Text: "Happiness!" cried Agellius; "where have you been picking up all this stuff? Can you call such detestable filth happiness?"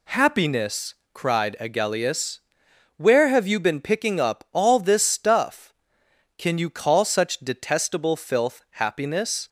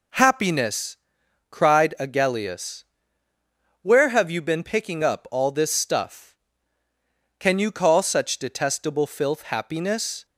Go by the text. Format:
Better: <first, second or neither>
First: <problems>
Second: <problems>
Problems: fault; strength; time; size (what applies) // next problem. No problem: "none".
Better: neither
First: none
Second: none